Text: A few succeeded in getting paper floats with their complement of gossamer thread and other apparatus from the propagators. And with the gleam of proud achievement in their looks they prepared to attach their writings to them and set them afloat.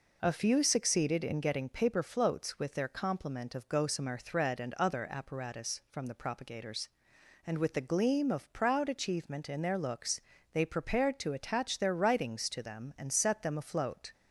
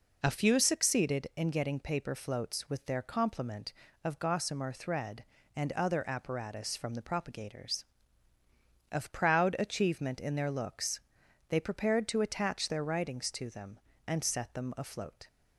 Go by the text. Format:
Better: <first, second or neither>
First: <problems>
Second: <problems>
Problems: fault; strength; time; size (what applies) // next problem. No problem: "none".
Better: first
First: pauses between "looks" and "they"; slight; at 10.1 s; 0.32 s long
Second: skips "And with the gleam"; at 8.3 s // pauses between "looks" and "they"; noticeable; at 11.0 s; 0.48 s long